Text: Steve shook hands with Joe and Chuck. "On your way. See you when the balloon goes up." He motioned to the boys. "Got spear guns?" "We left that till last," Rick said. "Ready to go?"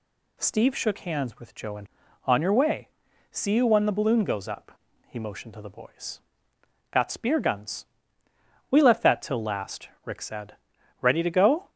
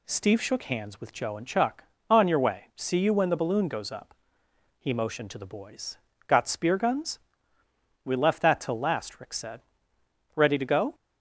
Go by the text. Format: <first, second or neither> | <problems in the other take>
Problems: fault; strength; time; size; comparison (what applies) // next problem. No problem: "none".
second | skips "Chuck"; at 2.0 s